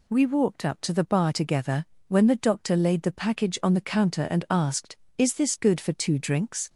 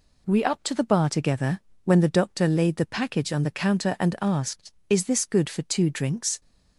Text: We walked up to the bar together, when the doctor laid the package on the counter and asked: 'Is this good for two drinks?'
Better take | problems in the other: first | skips "walked"; at 0.4 s

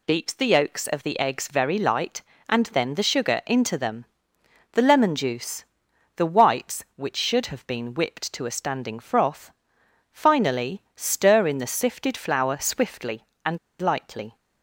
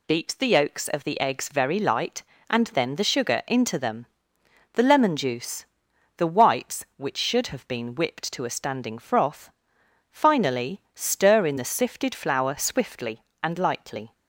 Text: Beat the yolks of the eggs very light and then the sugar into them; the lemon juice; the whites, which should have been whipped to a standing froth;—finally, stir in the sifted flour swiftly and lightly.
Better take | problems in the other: second | pauses between "and" and "lightly"; slight; at 13.5 s; 0.23 s long

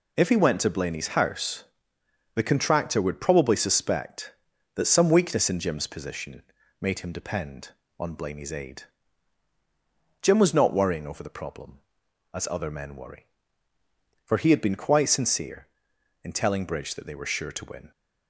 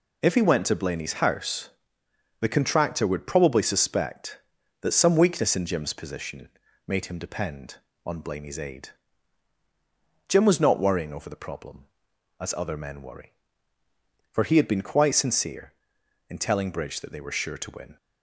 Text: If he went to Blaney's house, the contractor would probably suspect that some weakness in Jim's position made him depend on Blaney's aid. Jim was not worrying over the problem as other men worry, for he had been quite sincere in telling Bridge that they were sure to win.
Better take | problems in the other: neither | pauses between "position" and "made"; the same in both

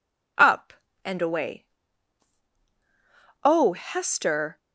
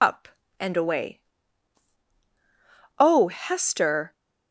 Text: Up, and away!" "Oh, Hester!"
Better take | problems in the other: first | loses the start of "Up"; at 0.0 s; 90 ms

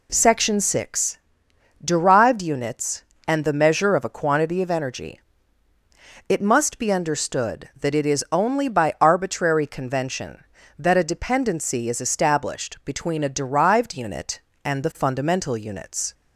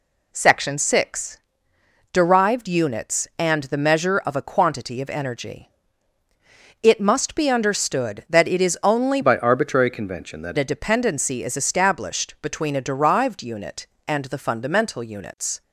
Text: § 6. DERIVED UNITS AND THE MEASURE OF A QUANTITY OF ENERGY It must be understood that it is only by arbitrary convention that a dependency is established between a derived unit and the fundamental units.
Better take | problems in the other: first | pauses between "ENERGY" and "It"; at 5.6 s; 1.1 s long; also in the first // changes voice from "by" to "that"; from 9.2 to 10.5 s; 1.3 s long

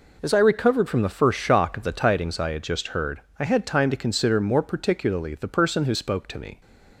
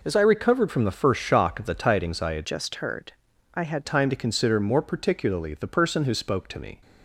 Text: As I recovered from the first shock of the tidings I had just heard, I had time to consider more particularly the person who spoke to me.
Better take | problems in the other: first | changes voice from "just" to "had"; from 2.4 to 3.8 s; 1.4 s long

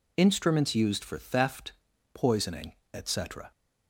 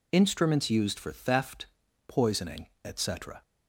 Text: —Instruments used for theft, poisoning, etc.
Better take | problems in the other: neither | none

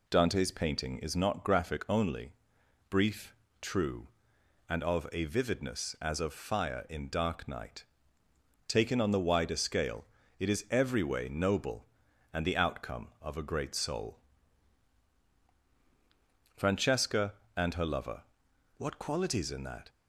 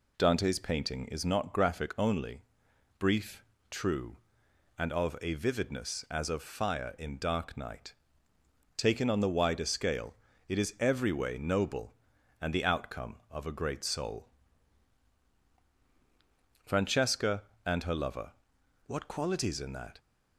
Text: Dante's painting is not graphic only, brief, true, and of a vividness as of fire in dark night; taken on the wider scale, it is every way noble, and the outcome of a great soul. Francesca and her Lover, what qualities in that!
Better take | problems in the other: neither | none

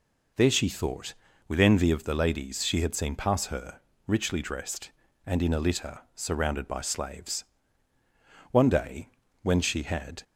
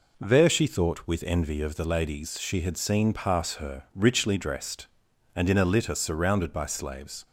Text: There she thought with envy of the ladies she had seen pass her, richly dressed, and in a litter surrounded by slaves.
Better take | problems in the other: second | pauses between "litter" and "surrounded"; slight; at 5.9 s; 0.16 s long // goes on to say "One day when she had"; strong; from 8.5 s on; 1.7 s long

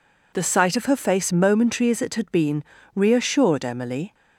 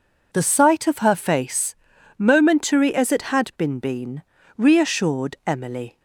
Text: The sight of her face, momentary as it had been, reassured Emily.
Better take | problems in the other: first | says "been" twice; at 3.7 s

